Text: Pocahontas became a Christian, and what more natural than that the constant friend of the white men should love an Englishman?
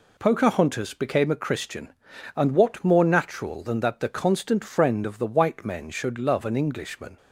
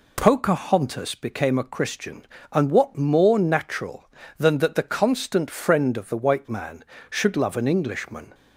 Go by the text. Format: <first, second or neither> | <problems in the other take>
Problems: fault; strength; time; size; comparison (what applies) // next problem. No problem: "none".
first | says "man" for "men"; at 6.5 s